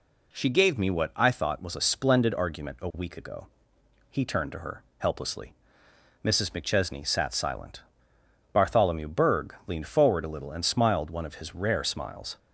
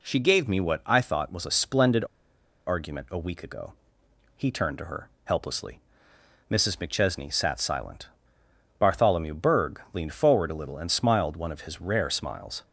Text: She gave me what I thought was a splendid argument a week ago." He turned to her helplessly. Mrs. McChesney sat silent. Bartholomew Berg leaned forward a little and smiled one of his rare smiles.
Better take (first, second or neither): first